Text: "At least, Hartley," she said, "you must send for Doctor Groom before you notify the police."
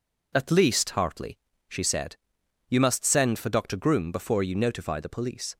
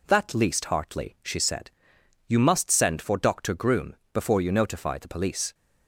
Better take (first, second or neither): first